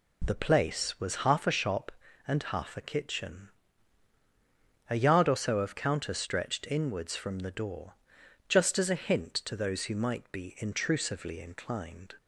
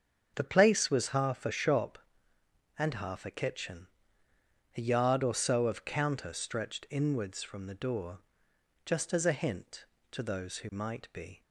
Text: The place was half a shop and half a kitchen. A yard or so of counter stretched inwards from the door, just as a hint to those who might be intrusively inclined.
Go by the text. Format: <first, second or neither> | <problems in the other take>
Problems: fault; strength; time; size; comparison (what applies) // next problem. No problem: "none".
first | starts louder than the rest; strong; until 1.3 s; 7 dB // stops before "intrusively inclined"; at 11.4 s